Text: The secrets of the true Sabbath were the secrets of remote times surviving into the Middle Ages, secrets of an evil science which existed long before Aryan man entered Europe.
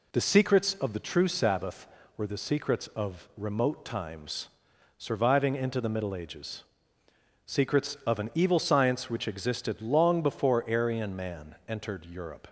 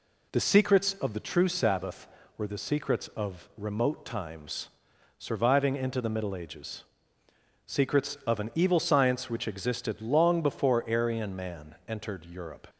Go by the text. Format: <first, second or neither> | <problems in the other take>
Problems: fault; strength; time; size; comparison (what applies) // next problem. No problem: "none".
neither | pauses between "times" and "surviving"; noticeable; the same in both